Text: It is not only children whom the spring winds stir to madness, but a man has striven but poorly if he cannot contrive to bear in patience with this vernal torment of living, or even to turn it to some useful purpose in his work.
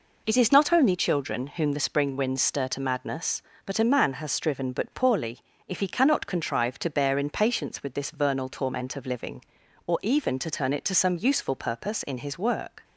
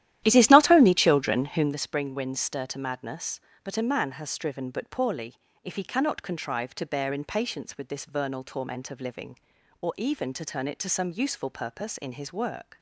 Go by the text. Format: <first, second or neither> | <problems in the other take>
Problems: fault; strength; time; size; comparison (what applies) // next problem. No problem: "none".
first | starts louder than the rest; strong; until 1.8 s; 13 dB // pauses between "poorly" and "if"; slight; at 5.3 s; 0.30 s long; slight in the first